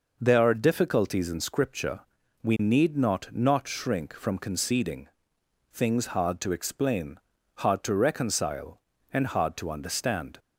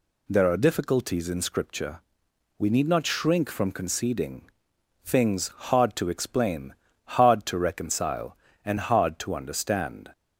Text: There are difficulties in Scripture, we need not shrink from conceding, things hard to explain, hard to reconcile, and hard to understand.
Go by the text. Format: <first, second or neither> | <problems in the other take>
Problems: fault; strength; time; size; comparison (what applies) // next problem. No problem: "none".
second | says "not" twice; at 3.3 s